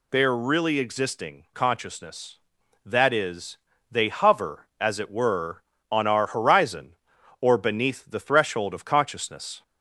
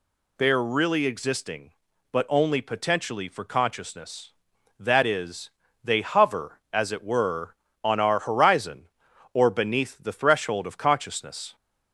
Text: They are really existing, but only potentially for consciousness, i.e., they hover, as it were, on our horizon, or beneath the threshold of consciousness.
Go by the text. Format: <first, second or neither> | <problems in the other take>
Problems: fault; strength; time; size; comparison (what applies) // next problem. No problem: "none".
second | skips "but only potentially for"; at 1.4 s